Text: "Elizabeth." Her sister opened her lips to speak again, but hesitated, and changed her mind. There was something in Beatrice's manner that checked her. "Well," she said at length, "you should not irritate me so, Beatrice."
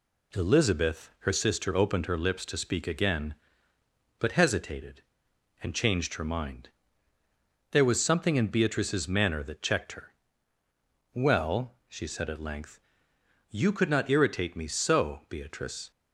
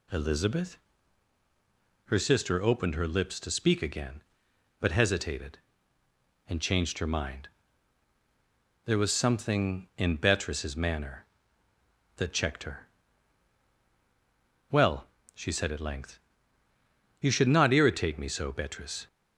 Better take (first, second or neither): second